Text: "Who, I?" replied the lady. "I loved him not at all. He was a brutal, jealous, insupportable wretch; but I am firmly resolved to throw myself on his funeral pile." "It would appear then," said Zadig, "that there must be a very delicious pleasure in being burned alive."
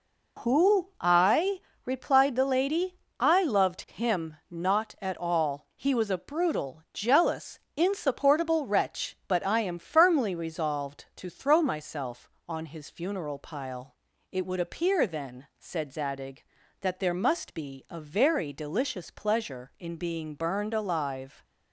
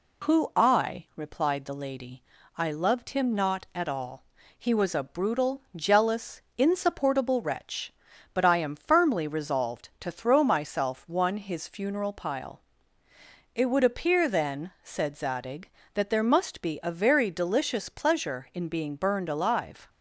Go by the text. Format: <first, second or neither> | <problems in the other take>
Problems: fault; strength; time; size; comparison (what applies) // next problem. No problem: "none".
first | says "one" for "on"; at 11.0 s